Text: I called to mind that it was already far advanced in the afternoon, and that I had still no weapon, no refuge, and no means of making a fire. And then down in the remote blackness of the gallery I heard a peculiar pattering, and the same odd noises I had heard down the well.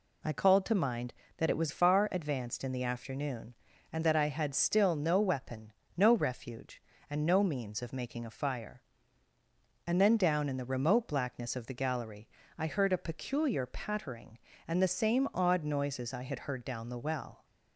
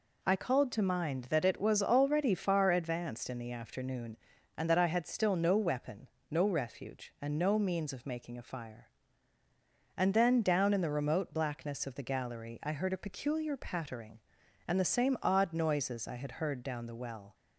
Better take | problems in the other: second | skips "already"; at 1.6 s // pauses between "gallery" and "I"; slight; at 12.2 s; 0.30 s long

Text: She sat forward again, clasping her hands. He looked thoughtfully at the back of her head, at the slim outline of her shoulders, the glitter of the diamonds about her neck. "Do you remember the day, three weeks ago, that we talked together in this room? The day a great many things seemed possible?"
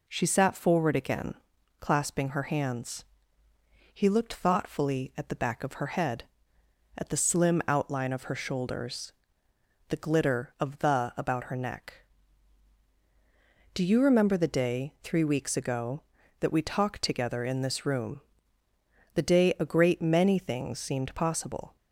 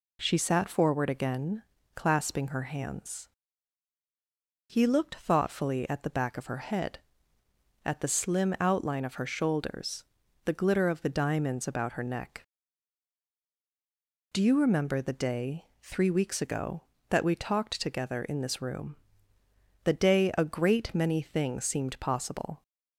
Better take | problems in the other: second | skips "diamonds"; at 11.1 s

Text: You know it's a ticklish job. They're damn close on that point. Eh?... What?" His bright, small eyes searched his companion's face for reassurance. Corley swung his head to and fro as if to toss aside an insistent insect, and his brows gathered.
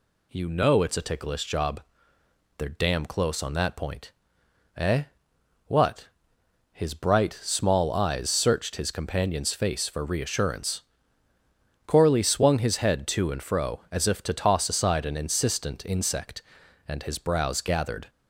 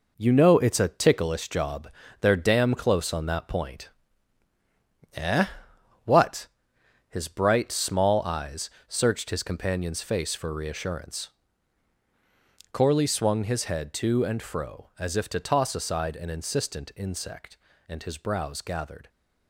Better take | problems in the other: first | gets quieter; throughout; 7 dB // pauses between "eyes" and "searched"; slight; at 8.7 s; 0.18 s long

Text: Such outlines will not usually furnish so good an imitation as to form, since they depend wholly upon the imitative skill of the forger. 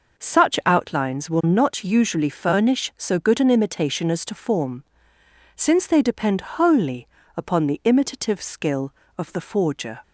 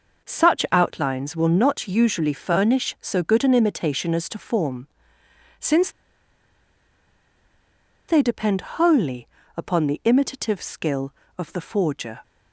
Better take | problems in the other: first | pauses between "since" and "they"; strong; at 5.9 s; 2.1 s long // pauses between "wholly" and "upon"; slight; at 9.2 s; 0.30 s long; slight in the first

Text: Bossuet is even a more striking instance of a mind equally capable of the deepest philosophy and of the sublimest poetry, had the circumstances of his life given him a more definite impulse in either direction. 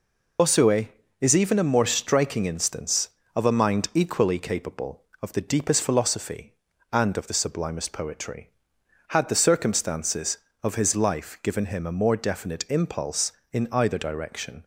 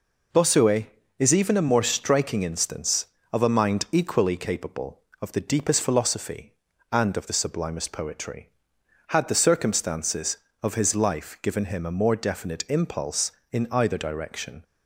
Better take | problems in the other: second | loses the start of "Bossuet"; at 0.3 s; 55 ms

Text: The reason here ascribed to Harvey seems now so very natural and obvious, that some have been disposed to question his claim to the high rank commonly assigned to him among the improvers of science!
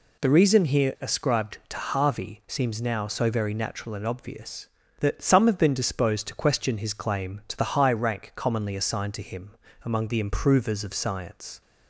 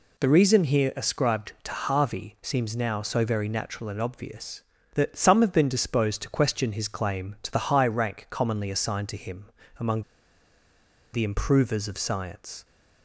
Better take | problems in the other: first | pauses between "him" and "among"; slight; at 9.5 s; 0.28 s long; slight in the first // pauses between "among" and "the"; at 10.0 s; 1.1 s long

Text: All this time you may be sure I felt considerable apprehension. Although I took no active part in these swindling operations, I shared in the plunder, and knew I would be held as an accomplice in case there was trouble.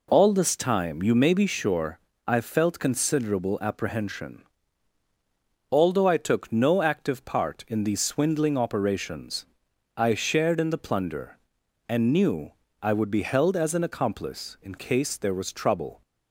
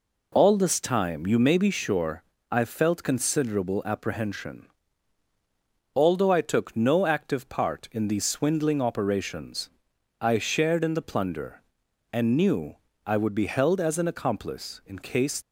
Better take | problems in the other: first | pauses between "sure" and "I"; slight; at 2.2 s; 0.26 s long; slight in the first // pauses between "knew" and "I"; slight; at 12.7 s; 0.28 s long; slight in the first // stops before "there was trouble"; at 15.4 s

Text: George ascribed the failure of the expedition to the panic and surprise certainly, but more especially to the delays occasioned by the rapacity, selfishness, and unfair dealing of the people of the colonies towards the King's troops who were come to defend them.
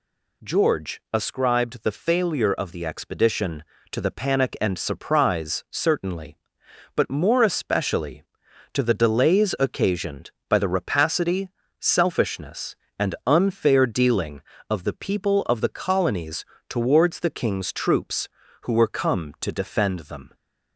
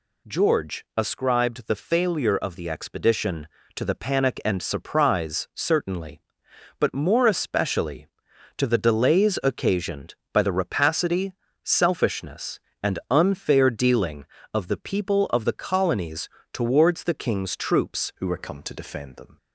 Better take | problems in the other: first | pauses between "colonies" and "towards"; slight; at 16.2 s; 0.24 s long; slight in the first // changes voice at "who"; from 18.1 s on; 1.2 s long

